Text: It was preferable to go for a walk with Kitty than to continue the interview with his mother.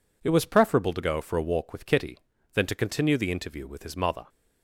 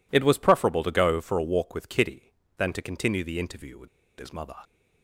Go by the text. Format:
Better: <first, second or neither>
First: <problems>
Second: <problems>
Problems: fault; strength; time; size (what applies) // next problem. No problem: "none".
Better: first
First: none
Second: pauses between "with" and "his"; slight; at 3.8 s; 0.32 s long